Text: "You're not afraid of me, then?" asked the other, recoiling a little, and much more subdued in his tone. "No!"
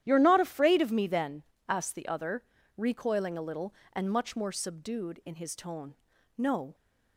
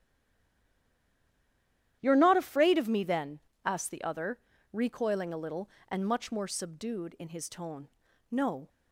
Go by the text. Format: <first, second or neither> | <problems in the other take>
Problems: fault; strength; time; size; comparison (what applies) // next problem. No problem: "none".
first | stays silent before the first word; noticeable; until 2.0 s; 2.0 s long // starts louder than the rest; strong; until 3.0 s; 11.5 dB; strong in the first